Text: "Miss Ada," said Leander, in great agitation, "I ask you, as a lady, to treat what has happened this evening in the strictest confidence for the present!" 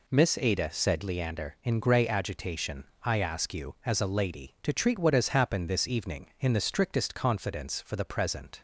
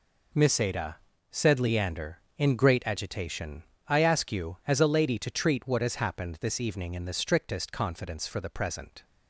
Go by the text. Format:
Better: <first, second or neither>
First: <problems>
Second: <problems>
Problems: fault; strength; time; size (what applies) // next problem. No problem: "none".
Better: second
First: says "grey" for "great"; at 1.8 s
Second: none